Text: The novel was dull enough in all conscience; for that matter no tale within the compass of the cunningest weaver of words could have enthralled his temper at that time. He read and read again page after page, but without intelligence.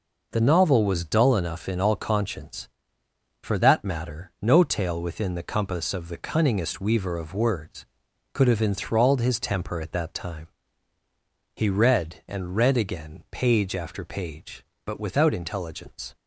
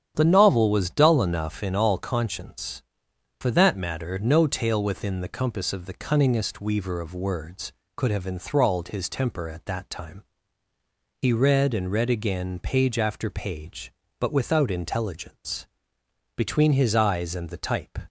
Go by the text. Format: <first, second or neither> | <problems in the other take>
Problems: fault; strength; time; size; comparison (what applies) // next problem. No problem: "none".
first | starts louder than the rest; strong; until 1.1 s; 9.5 dB // goes on to say "Between his eyes and the type"; from 16.3 s on; 1.6 s long